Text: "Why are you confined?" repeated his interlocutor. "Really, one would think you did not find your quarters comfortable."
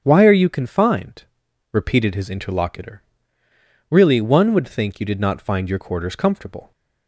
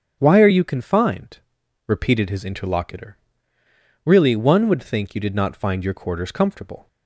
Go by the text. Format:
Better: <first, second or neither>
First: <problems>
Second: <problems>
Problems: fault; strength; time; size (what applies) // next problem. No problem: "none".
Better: neither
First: starts louder than the rest; strong; until 1.0 s; 8 dB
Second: starts louder than the rest; strong; until 1.2 s; 8.5 dB